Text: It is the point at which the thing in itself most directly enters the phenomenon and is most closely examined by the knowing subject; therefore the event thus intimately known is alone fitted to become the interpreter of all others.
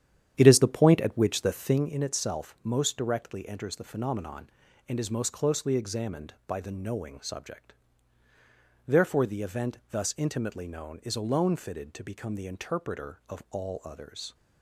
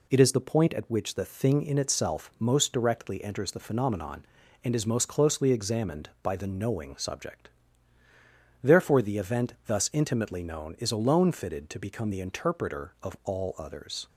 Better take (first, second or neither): second